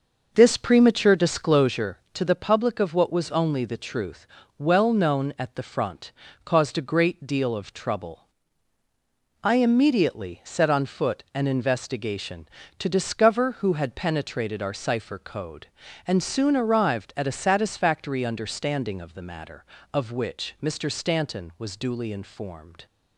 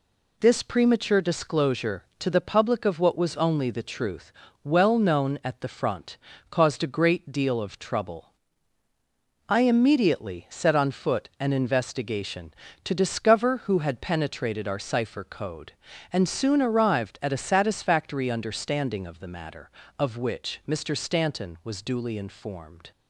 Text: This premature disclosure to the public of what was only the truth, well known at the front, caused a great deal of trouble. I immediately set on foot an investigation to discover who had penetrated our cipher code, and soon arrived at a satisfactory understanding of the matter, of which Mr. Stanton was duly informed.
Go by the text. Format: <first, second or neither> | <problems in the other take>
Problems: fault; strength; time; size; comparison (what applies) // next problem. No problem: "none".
second | starts louder than the rest; noticeable; until 1.9 s; 6 dB